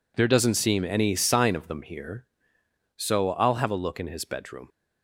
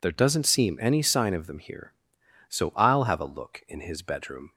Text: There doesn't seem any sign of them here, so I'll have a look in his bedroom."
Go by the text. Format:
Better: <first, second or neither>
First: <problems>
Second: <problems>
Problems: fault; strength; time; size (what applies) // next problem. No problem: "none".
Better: neither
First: none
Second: none